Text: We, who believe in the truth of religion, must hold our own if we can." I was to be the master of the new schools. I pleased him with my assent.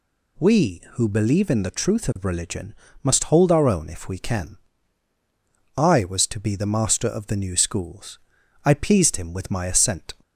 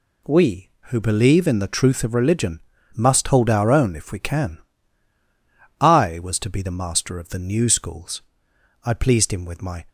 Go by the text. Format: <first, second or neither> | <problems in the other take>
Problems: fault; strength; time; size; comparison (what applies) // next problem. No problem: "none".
first | stops before "assent"; at 9.8 s